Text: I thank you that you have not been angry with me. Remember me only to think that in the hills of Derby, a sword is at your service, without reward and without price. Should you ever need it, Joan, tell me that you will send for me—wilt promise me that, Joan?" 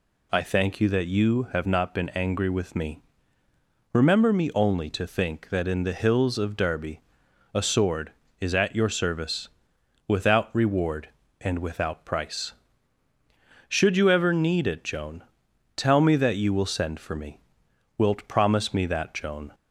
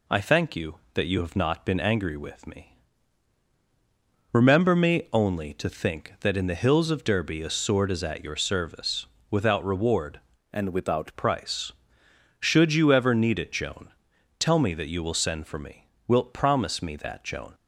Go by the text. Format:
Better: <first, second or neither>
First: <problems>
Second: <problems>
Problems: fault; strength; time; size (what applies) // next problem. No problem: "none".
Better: first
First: none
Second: changes voice from "and" to "without"; from 10.5 to 11.1 s; 0.6 s long